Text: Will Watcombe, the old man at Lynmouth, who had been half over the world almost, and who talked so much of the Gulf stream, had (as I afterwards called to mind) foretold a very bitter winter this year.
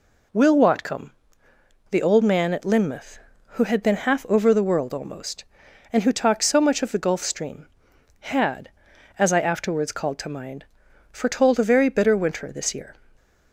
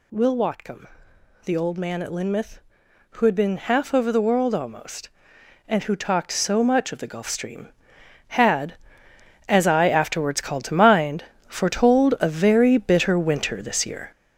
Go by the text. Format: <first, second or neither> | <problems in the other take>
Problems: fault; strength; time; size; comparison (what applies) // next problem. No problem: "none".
first | gets louder; throughout; 7 dB